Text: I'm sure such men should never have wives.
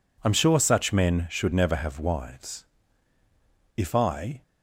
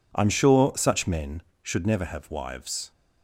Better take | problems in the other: second | goes on to say "If I"; noticeable; from 3.7 s on; 0.66 s long

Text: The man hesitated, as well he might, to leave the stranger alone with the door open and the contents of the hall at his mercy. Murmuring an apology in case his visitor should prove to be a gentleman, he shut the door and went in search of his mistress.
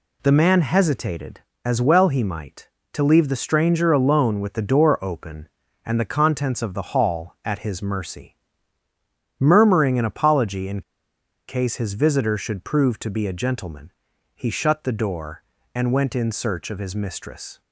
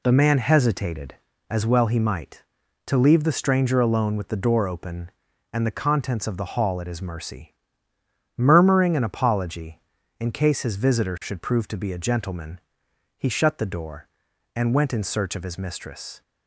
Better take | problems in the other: second | pauses between "in" and "case"; noticeable; at 10.8 s; 0.66 s long

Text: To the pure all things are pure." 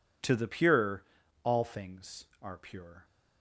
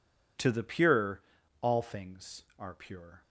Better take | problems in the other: neither | pauses between "pure" and "all"; the same in both

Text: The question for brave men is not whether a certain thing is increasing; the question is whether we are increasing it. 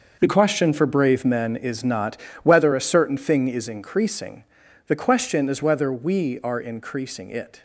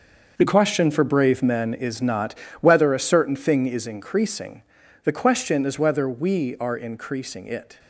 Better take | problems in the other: neither | starts louder than the rest; the same in both // pauses between "not" and "whether"; slight; the same in both

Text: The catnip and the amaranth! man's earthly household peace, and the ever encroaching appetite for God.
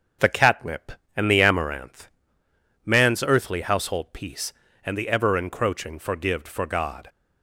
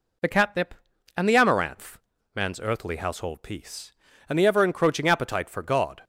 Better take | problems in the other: second | starts louder than the rest; strong; until 1.4 s; 7.5 dB // says "forgived" for "appetite"; at 5.9 s

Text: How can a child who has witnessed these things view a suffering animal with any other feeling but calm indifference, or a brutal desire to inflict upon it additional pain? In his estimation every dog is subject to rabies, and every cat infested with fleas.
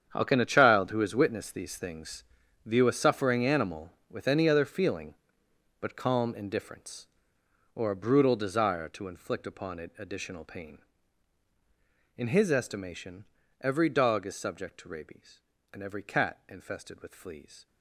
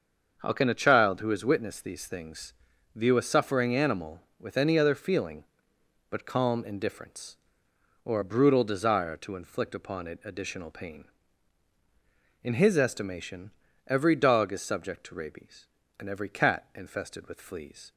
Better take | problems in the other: second | gets quieter; strong; throughout; 13.5 dB // starts louder than the rest; strong; until 1.1 s; 8 dB; also in the second // pauses between "things" and "view"; at 2.2 s; 0.40 s long; also in the second // pauses between "estimation" and "every"; slight; at 13.2 s; 0.34 s long; slight in the second

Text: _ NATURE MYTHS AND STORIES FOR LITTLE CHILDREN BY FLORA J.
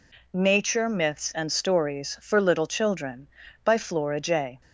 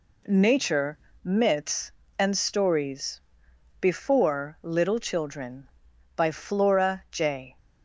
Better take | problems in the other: first | pauses between "NATURE" and "MYTHS"; slight; at 0.9 s; 0.28 s long // says "Before" for "FOR"; at 3.8 s

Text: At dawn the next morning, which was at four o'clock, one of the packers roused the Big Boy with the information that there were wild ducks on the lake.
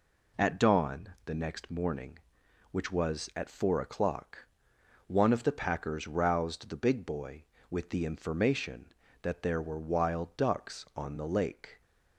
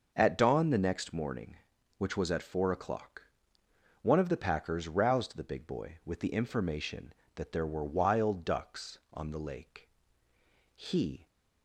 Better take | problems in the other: first | starts louder than the rest; noticeable; until 1.1 s; 6 dB // goes on to say "He"; from 10.7 s on; 0.52 s long

